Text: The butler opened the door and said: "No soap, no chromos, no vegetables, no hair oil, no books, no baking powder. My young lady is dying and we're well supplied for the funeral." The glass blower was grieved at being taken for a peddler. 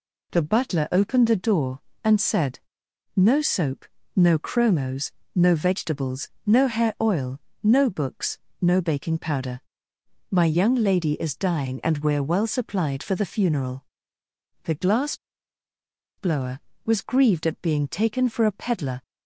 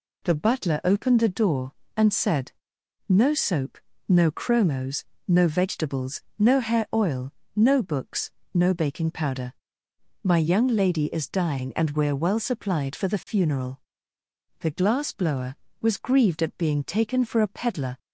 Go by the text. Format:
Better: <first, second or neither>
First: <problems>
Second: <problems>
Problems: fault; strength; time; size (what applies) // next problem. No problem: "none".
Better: second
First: pauses between "glass" and "blower"; at 15.1 s; 1.0 s long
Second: none